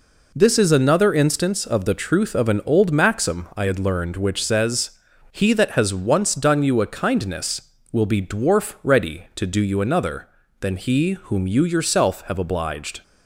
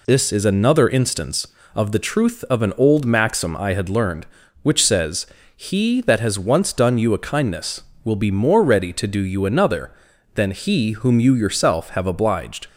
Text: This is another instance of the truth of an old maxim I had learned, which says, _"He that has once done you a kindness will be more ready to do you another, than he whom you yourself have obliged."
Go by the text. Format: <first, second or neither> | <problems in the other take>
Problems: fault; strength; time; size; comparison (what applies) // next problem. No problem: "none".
second | says "dwarf" for "more"; at 8.2 s